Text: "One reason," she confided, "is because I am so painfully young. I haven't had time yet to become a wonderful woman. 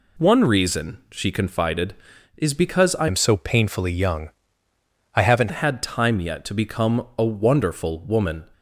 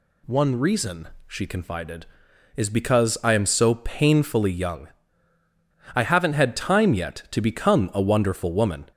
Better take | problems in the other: second | changes voice from "am" to "haven't"; from 3.0 to 5.5 s; 2.5 s long

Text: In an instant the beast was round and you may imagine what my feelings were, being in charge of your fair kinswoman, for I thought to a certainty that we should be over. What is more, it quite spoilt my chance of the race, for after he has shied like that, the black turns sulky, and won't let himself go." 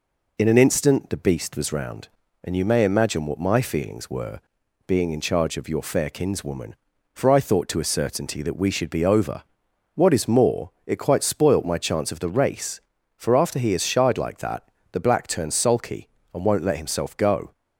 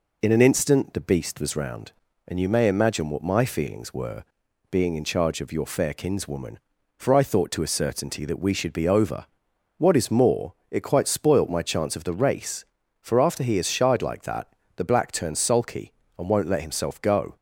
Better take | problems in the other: neither | none

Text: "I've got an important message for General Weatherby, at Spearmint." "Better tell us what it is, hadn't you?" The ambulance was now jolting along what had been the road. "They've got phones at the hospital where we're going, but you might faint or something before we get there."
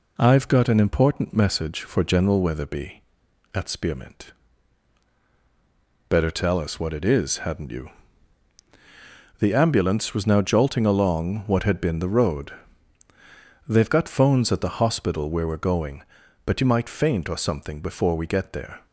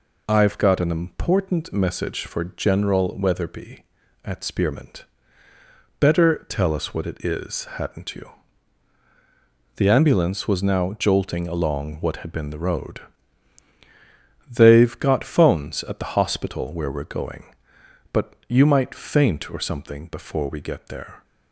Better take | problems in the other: neither | none

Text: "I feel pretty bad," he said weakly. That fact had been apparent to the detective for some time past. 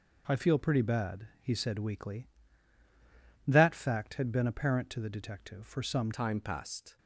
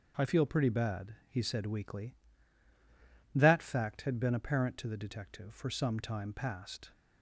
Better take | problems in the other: second | changes voice at "time"; from 6.1 s on; 0.8 s long

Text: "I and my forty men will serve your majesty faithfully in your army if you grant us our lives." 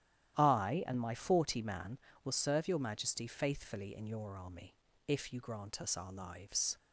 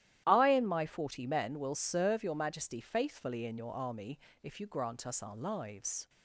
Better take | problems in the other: second | starts louder than the rest; strong; until 1.4 s; 11.5 dB; strong in the second // says "man" for "men"; at 1.6 s // pauses between "army" and "if"; slight; at 4.7 s; 0.30 s long; slight in the second

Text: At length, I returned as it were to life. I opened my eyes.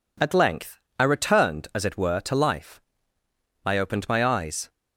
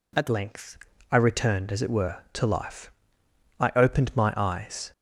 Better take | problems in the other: first | changes voice at "length"; from 0.2 s on; 4.7 s long

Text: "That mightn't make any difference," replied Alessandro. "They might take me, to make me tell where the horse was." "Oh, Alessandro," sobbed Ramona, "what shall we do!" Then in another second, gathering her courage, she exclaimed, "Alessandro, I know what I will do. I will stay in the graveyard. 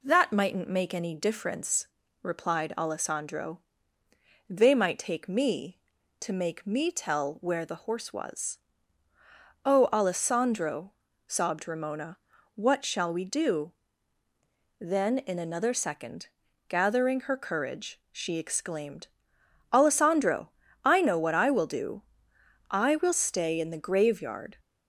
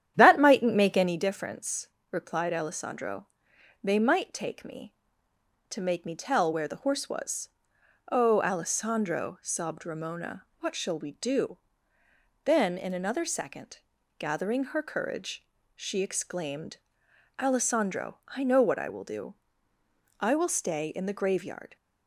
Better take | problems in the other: first | starts louder than the rest; strong; until 1.2 s; 10 dB

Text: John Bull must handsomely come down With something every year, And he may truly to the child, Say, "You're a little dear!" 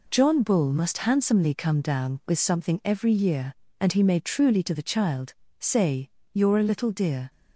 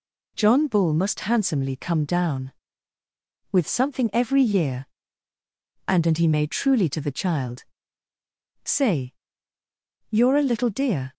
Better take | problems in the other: first | says "And" twice; at 6.0 s

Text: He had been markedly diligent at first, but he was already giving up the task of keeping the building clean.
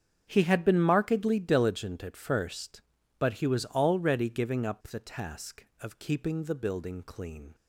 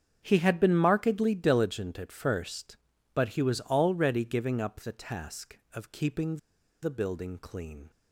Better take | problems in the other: first | starts louder than the rest; strong; until 1.2 s; 7.5 dB; strong in the first // pauses between "keeping" and "the"; at 6.3 s; 0.44 s long

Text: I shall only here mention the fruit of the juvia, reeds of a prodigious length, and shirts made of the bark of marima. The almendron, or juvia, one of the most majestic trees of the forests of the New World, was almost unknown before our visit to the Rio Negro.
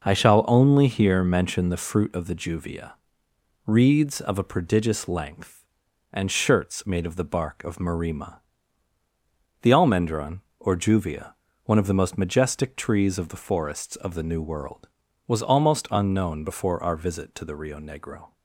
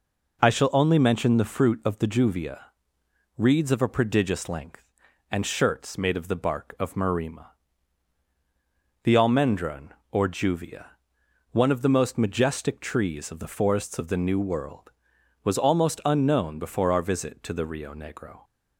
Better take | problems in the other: first | skips "here"; at 0.9 s

